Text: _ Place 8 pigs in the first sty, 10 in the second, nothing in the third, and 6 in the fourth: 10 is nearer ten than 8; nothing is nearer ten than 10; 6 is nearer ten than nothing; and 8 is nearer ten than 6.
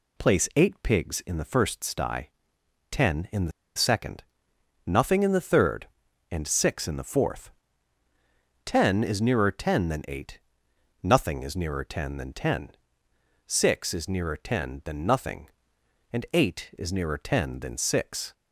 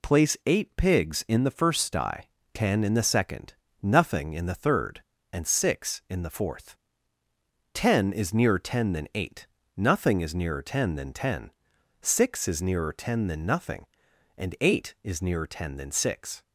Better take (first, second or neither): second